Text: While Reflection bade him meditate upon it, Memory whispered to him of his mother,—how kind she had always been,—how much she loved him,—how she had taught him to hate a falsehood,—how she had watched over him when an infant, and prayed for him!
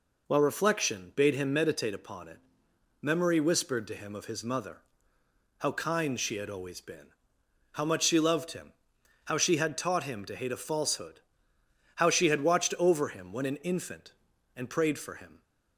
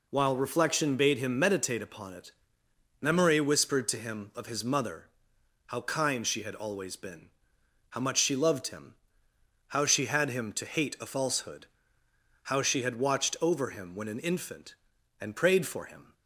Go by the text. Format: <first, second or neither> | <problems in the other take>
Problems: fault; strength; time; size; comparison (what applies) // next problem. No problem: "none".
first | skips "taught"; at 10.2 s